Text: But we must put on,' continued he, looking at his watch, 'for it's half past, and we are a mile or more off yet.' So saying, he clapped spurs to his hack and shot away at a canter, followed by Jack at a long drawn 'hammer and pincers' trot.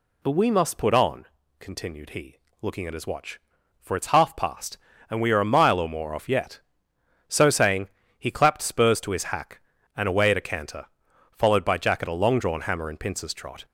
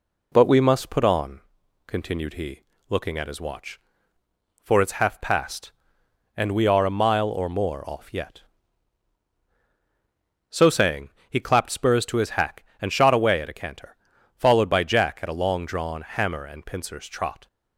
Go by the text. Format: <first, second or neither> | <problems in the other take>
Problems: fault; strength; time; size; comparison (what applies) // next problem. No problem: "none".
second | skips "shot"; at 10.0 s